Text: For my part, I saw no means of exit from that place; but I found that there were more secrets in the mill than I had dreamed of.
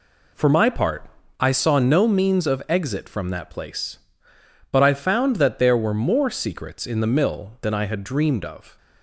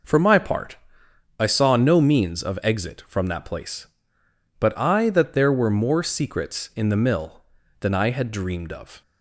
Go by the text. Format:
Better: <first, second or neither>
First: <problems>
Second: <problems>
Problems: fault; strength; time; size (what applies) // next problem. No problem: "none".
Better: first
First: none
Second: skips "found"; at 5.0 s